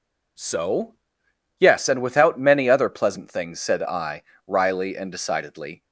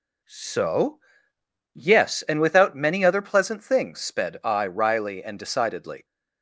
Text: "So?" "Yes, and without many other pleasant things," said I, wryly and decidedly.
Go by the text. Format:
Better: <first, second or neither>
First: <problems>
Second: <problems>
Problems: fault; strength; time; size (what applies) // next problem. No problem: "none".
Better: first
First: none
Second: says "sped" for "said"; at 3.9 s